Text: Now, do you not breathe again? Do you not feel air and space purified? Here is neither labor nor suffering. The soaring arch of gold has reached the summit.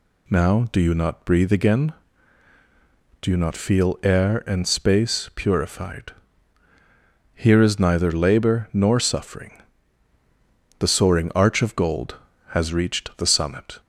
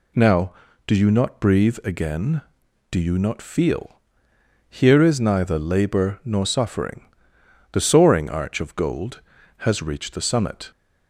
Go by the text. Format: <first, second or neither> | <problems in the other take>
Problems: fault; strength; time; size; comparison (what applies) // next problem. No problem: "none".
first | skips "air and space purified"; at 4.3 s